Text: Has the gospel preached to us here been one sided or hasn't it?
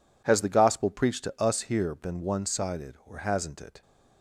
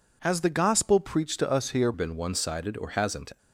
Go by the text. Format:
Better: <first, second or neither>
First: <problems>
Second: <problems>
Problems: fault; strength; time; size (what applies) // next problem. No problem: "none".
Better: first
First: none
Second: changes voice from "been" to "hasn't"; from 1.9 to 3.3 s; 1.4 s long